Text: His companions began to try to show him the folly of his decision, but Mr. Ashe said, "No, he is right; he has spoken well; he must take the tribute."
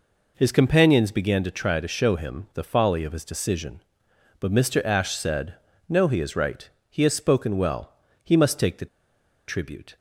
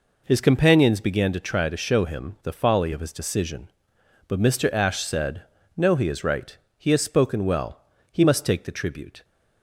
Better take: second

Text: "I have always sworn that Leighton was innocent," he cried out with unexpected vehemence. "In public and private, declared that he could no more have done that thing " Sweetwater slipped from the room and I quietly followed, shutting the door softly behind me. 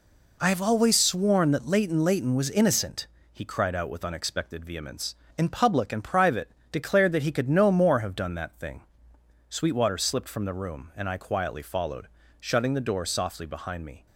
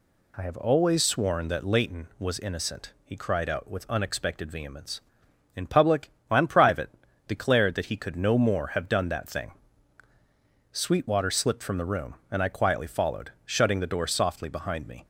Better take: second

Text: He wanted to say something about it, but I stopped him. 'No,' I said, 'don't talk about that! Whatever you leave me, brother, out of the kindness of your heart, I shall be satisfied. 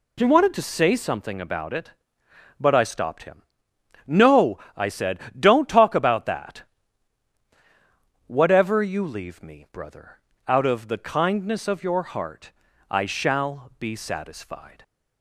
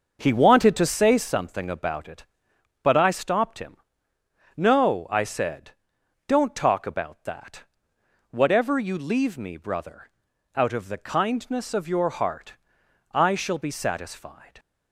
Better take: first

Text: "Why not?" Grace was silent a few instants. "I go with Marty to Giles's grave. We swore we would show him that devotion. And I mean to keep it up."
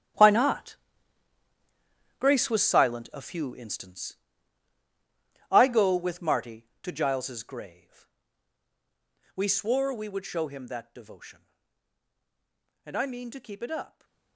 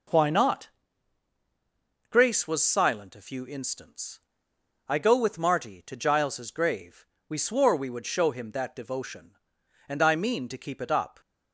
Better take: second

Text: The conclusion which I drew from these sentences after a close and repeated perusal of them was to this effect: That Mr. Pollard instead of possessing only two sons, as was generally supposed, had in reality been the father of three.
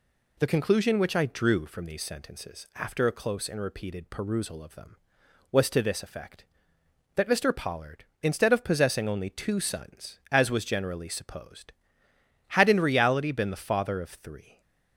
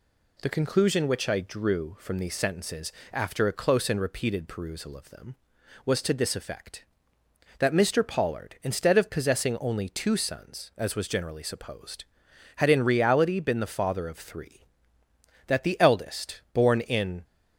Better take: first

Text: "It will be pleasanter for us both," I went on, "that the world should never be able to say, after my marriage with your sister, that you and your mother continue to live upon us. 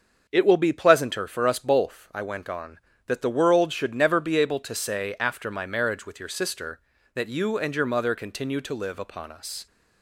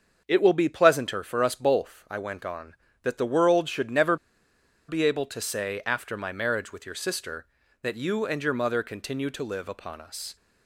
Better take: first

